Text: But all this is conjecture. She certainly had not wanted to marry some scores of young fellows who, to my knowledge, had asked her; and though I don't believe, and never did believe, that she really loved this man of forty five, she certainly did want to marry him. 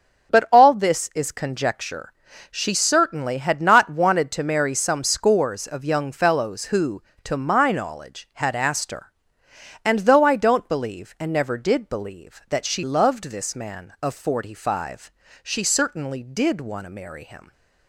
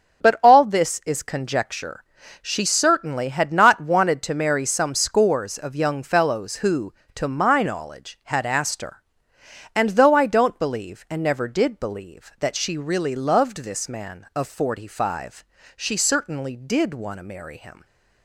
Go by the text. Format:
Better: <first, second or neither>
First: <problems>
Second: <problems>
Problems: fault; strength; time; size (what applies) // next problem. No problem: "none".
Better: second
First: starts louder than the rest; until 1.3 s; 7 dB // skips "really"; at 12.8 s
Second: starts louder than the rest; until 1.3 s; 7 dB